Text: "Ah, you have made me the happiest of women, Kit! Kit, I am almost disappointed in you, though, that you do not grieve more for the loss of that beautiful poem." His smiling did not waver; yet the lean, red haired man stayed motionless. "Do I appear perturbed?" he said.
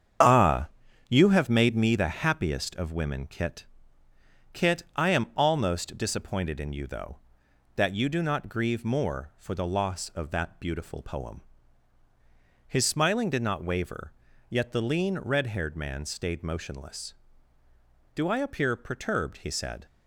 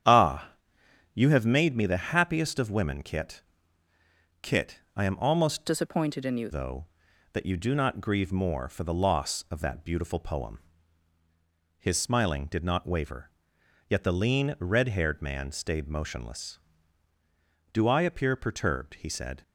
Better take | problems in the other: first | starts louder than the rest; strong; until 1.6 s; 9 dB; strong in the first // changes voice from "disappointed" to "you"; from 5.6 to 6.4 s; 0.8 s long

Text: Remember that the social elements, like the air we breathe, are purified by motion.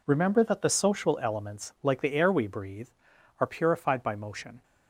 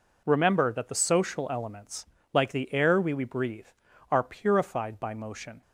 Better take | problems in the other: first | says "we" twice; at 3.1 s

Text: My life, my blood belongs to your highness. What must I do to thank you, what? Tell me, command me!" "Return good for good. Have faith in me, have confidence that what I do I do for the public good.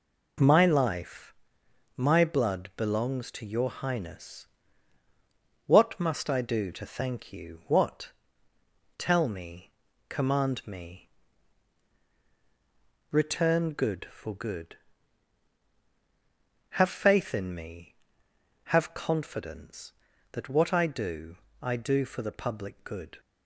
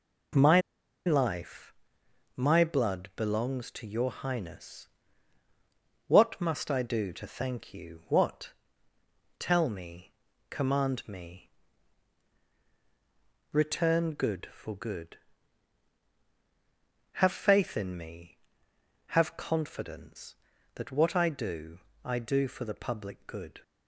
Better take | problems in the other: first | pauses between "My" and "life"; noticeable; at 0.5 s; 0.46 s long // pauses between "do" and "I"; slight; at 21.8 s; 0.24 s long; slight in the first

